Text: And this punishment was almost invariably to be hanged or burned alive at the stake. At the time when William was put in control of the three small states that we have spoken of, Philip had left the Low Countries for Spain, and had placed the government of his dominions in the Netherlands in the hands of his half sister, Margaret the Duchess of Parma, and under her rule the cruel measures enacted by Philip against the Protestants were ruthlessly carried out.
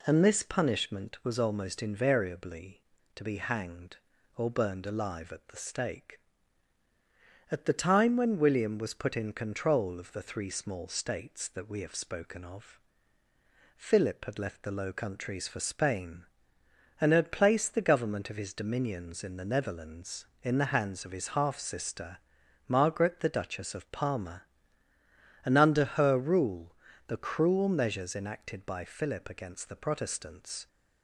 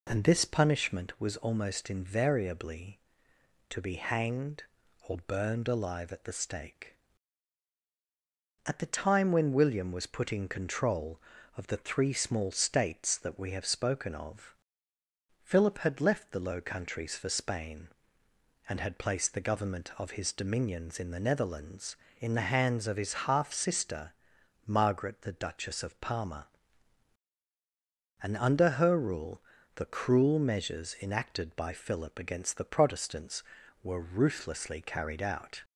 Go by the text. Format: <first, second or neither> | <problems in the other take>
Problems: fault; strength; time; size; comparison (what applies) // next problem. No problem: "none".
second | pauses between "rule" and "the"; slight; at 26.7 s; 0.34 s long; slight in the second // stops before "were ruthlessly carried out"; at 30.6 s